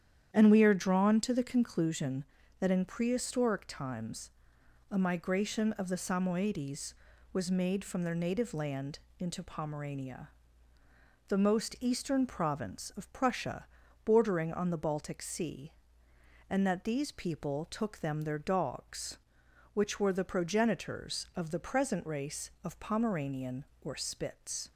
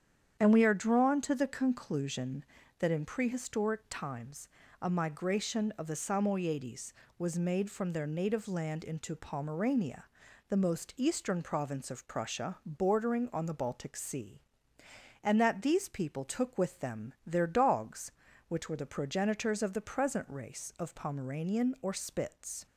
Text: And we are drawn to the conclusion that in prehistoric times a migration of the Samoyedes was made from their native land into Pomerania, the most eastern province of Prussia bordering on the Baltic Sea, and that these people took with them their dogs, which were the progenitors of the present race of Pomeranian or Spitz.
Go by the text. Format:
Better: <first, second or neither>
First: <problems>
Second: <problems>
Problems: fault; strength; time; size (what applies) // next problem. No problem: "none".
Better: second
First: starts louder than the rest; strong; until 1.3 s; 9.5 dB // pauses between "times" and "a"; noticeable; at 4.2 s; 0.60 s long // pauses between "land" and "into"; slight; at 8.9 s; 0.20 s long // pauses between "Prussia" and "bordering"; at 13.6 s; 0.40 s long // skips "with"; at 17.9 s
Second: starts louder than the rest; strong; until 1.4 s; 8.5 dB // pauses between "times" and "a"; slight; at 4.4 s; 0.34 s long